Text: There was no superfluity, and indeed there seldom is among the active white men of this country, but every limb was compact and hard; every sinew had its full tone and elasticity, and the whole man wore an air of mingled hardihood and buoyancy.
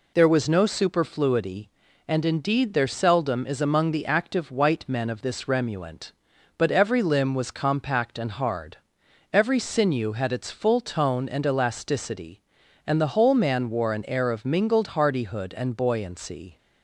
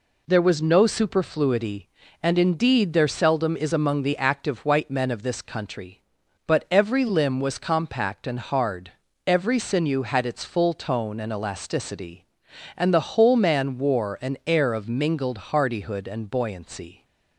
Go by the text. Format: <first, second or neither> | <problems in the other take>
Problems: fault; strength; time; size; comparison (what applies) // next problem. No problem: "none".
second | says "remuant" for "country"; at 5.4 s